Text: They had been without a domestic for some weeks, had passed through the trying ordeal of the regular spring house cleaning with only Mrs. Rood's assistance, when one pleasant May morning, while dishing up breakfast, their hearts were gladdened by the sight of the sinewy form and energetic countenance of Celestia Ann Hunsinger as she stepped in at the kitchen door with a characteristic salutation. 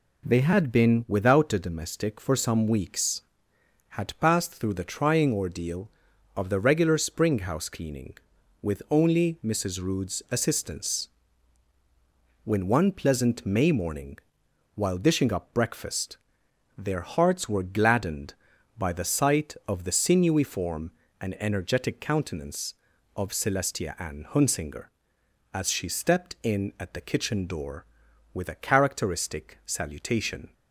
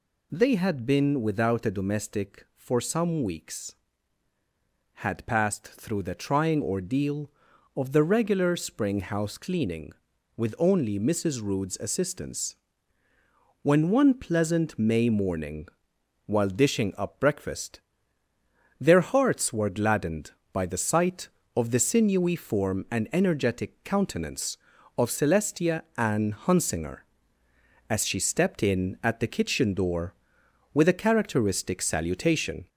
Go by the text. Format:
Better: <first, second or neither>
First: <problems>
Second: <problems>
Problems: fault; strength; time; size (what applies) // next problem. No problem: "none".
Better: first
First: none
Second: gets louder; slight; throughout; 3 dB